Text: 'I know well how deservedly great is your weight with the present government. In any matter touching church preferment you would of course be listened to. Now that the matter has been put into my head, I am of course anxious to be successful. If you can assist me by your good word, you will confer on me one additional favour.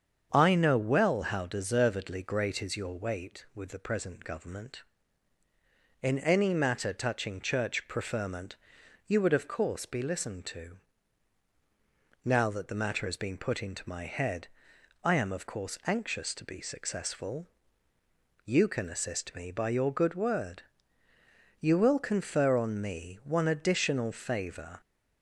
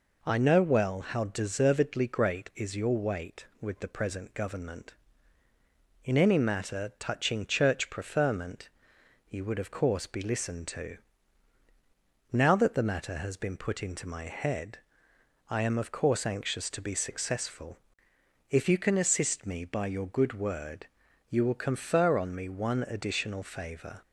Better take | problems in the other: second | starts louder than the rest; strong; until 1.3 s; 7.5 dB // pauses between "preferment" and "you"; noticeable; at 8.5 s; 0.52 s long; noticeable in the second // skips "If"; at 17.9 s

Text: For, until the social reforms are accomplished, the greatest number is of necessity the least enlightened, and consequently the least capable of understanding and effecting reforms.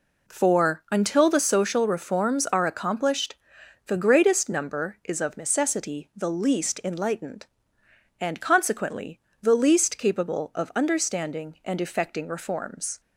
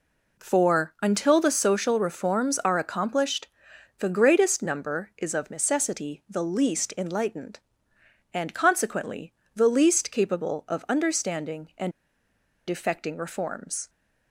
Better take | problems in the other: first | pauses between "consequently" and "the"; slight; at 9.3 s; 0.22 s long; slight in the first // pauses between "and" and "effecting"; noticeable; at 11.9 s; 0.77 s long

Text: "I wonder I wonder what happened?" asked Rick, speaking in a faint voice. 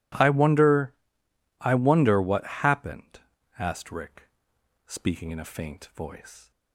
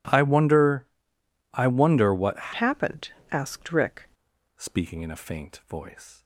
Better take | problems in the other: first | pauses between "wonder" and "I"; noticeable; at 0.8 s; 0.66 s long; noticeable in the first // changes voice from "happened" to "Rick"; from 2.5 to 4.0 s; 1.5 s long

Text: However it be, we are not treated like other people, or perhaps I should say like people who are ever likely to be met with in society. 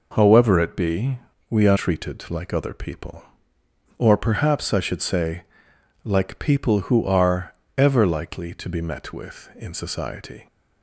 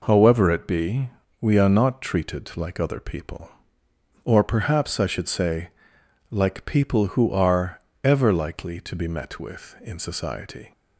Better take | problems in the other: second | skips "not"; at 1.7 s // pauses between "say" and "like"; noticeable; at 5.4 s; 0.60 s long; noticeable in the second // pauses between "are" and "ever"; slight; at 7.5 s; 0.24 s long; slight in the second

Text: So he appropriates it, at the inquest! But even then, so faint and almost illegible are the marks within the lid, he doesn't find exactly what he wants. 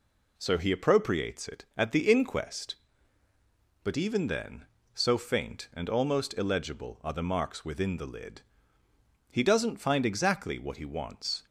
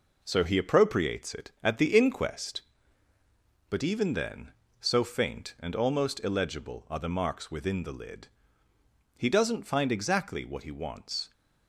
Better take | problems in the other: first | gets quieter; noticeable; throughout; 5.5 dB

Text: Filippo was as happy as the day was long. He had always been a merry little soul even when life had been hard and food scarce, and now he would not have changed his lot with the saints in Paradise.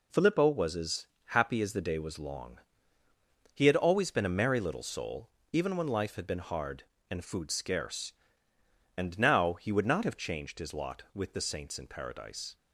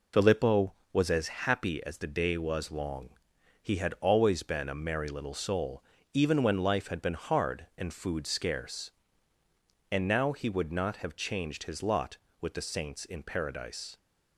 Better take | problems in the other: first | loses the start of "Filippo"; at 0.1 s; 45 ms // pauses between "as" and "happy"; slight; at 1.2 s; 0.18 s long; slight in the first // pauses between "soul" and "even"; slight; at 5.8 s; 0.30 s long; slight in the first

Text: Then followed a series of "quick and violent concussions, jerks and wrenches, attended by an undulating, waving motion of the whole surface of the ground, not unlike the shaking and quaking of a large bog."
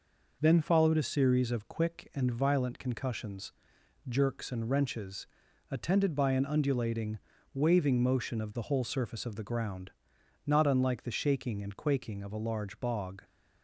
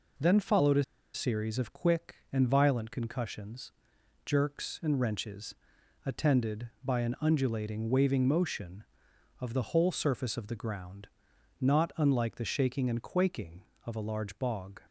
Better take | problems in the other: first | pauses between "a" and "series"; slight; at 0.8 s; 0.31 s long

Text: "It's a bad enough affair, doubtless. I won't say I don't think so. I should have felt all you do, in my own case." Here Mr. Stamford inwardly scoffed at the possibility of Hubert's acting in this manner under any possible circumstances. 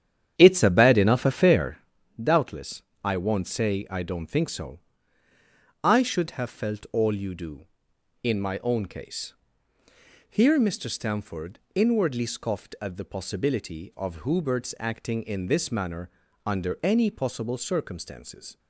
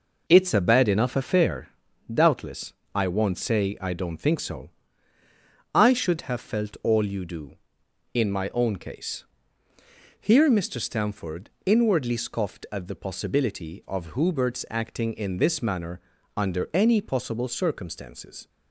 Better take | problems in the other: second | starts louder than the rest; strong; until 1.9 s; 9 dB // pauses between "Stamford" and "inwardly"; slight; at 11.5 s; 0.16 s long; slight in the second // pauses between "manner" and "under"; slight; at 16.0 s; 0.34 s long; slight in the second

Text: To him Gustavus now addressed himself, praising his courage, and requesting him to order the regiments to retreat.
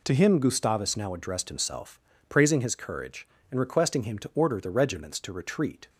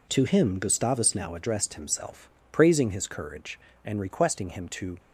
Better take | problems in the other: first | stops before "order the regiments to retreat"; at 4.9 s

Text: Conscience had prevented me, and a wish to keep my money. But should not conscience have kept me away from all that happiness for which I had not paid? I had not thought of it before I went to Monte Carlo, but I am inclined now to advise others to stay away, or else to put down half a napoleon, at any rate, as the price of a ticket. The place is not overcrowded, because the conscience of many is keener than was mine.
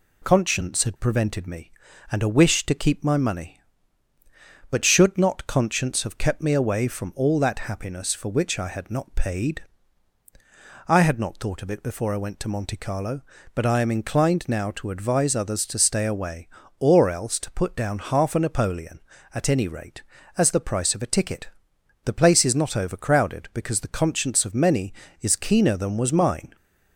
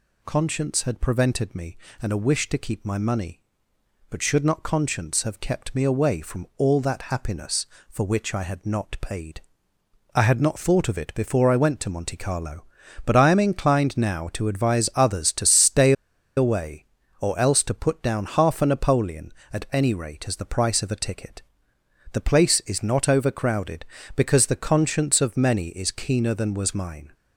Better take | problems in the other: first | pauses between "stay" and "away"; at 15.9 s; 0.44 s long

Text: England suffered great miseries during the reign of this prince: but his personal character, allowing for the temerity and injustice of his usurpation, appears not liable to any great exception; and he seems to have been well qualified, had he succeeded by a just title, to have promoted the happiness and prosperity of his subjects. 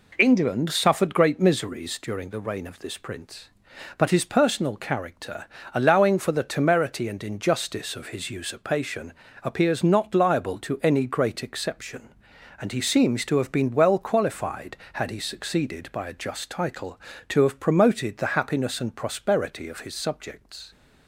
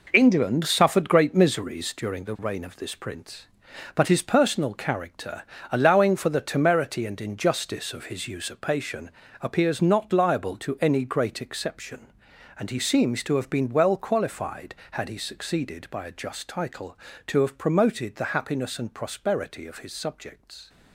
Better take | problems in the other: first | gets quieter; strong; throughout; 8.5 dB

